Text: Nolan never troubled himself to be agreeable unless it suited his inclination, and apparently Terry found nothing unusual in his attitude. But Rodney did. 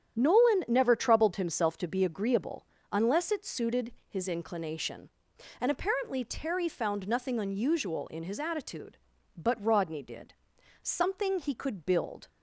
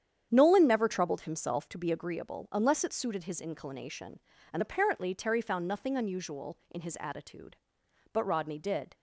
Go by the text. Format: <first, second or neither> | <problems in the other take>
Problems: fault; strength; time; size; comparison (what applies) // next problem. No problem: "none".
second | starts louder than the rest; strong; until 1.2 s; 9 dB; strong in the second // pauses between "agreeable" and "unless"; slight; at 2.6 s; 0.26 s long // pauses between "suited" and "his"; slight; at 3.9 s; 0.16 s long // goes on to say "Something he could build"; strong; from 10.4 s on; 1.8 s long